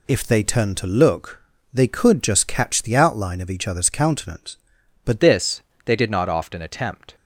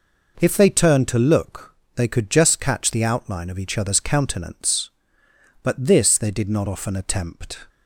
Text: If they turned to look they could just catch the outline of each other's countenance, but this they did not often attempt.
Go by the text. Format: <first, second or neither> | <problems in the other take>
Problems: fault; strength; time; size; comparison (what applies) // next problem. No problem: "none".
second | pauses between "look" and "they"; slight; at 1.4 s; 0.32 s long; slight in the second // changes voice at "this"; from 5.2 s on; 1.9 s long // pauses between "this" and "they"; slight; at 5.6 s; 0.24 s long